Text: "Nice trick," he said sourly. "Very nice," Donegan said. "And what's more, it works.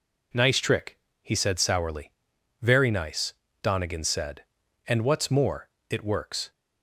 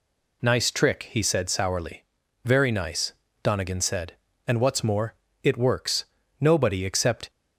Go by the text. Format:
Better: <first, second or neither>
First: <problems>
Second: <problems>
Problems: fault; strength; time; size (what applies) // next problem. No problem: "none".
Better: first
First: none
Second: goes on to say "Nobody except"; noticeable; from 6.3 s on; 0.90 s long